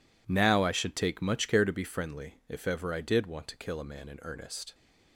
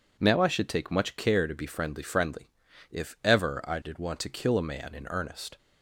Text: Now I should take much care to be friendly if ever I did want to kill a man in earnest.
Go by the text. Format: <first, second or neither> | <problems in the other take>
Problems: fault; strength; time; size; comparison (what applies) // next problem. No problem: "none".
first | says "friendly" twice; at 2.0 s